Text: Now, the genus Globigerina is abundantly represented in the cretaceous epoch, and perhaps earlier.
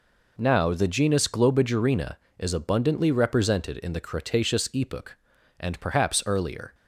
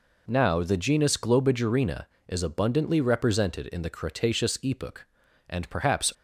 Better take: first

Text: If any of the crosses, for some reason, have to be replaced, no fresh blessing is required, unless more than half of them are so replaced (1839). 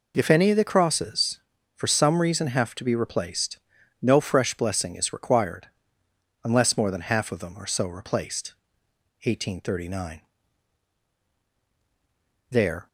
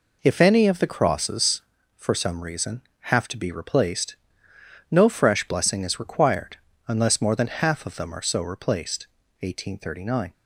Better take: second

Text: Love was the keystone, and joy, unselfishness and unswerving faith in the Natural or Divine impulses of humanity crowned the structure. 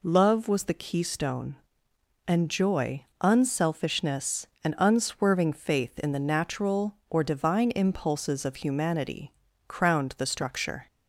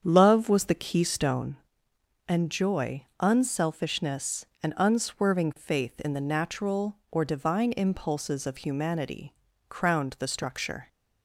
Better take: first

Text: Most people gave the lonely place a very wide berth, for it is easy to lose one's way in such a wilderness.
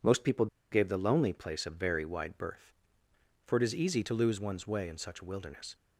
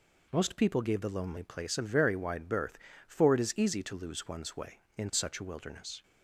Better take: second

